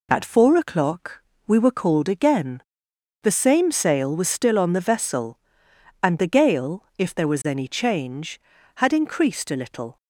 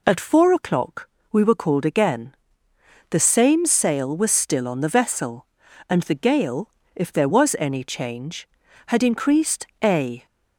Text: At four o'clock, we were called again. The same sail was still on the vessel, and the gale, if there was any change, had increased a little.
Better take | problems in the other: first | pauses between "increased" and "a"; slight; at 9.6 s; 0.16 s long // stops before "little"; at 10.2 s

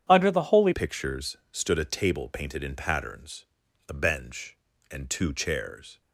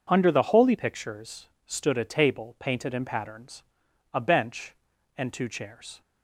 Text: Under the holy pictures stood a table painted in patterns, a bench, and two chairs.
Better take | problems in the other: second | starts louder than the rest; strong; until 1.0 s; 9 dB // changes voice at "pictures"; from 0.7 s on; 5.3 s long // pauses between "pictures" and "stood"; slight; at 1.3 s; 0.16 s long; slight in the second

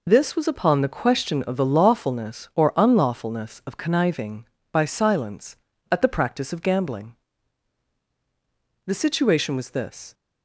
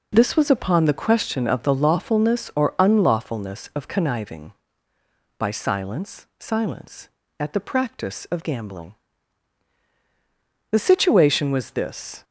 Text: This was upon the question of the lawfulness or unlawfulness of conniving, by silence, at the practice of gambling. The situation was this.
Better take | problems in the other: first | says "silence" twice; at 6.3 s

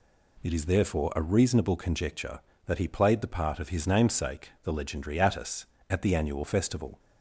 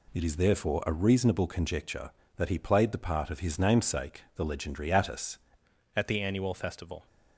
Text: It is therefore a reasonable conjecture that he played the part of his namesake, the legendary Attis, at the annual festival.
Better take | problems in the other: first | changes voice at "at"; from 5.9 s on; 1.1 s long

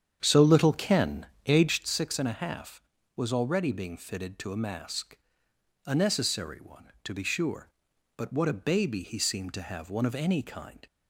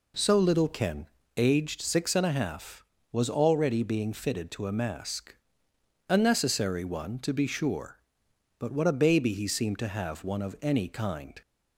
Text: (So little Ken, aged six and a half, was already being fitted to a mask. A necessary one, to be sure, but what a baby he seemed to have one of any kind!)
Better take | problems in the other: second | starts louder than the rest; strong; until 1.9 s; 8.5 dB

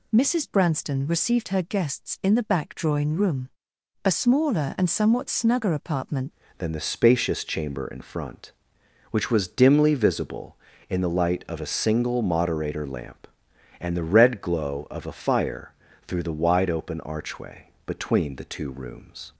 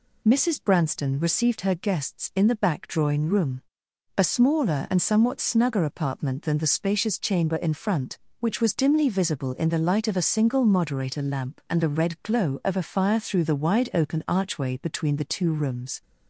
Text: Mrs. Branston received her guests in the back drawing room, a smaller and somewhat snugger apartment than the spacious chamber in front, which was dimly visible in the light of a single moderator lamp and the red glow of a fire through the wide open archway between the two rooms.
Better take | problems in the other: second | changes voice at "than"; from 6.5 s on; 12.8 s long // pauses between "fire" and "through"; slight; at 15.7 s; 0.36 s long // pauses between "archway" and "between"; slight; at 17.6 s; 0.18 s long

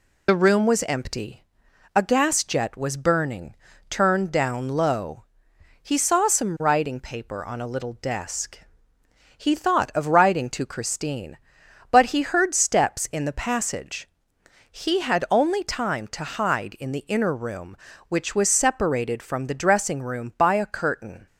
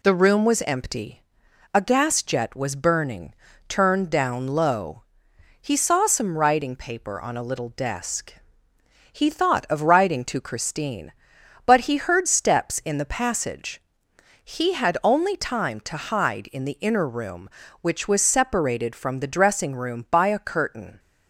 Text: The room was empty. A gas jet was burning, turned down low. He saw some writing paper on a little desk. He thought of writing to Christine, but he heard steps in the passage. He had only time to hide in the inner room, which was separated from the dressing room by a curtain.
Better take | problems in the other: second | loses the start of "The"; at 0.2 s; 35 ms

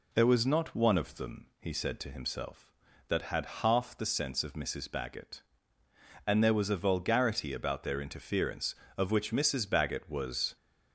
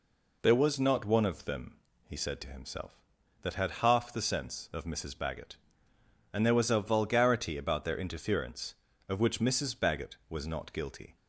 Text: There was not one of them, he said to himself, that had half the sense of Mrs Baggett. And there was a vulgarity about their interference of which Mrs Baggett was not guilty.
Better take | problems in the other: second | stops before "not guilty"; at 10.5 s

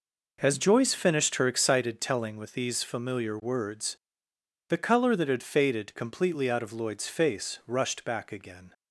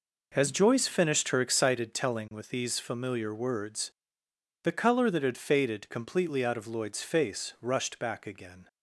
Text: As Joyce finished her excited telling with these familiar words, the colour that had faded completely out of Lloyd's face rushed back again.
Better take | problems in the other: neither | none

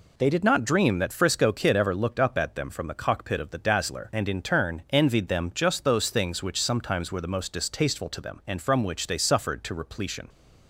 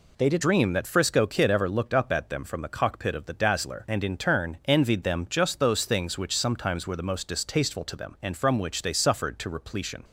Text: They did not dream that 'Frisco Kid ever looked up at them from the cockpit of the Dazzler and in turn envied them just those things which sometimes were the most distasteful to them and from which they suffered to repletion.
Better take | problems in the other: first | skips "not"; at 0.4 s

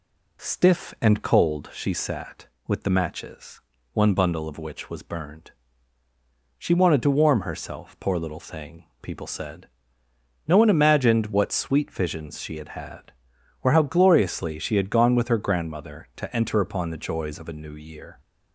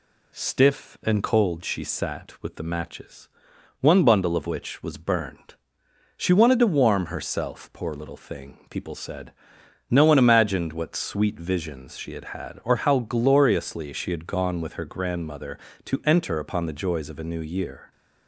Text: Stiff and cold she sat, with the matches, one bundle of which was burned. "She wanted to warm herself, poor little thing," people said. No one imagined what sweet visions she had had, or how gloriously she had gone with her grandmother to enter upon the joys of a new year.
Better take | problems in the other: neither | none

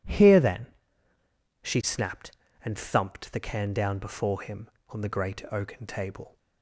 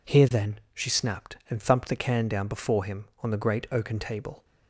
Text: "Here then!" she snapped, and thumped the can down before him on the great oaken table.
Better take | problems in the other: neither | none

